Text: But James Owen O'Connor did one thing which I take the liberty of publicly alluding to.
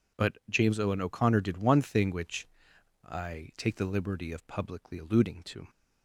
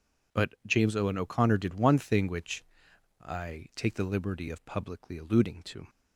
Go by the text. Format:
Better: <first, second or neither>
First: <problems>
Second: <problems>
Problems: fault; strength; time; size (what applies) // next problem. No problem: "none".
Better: neither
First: pauses between "which" and "I"; noticeable; at 2.4 s; 0.58 s long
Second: pauses between "which" and "I"; noticeable; at 2.6 s; 0.58 s long